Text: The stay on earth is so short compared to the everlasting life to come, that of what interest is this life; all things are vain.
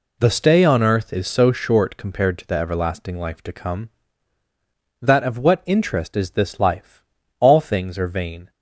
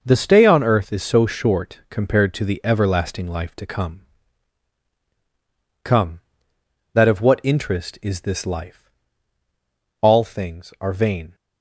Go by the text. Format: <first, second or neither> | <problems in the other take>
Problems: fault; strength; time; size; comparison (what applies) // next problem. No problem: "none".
first | says "come" twice; at 5.8 s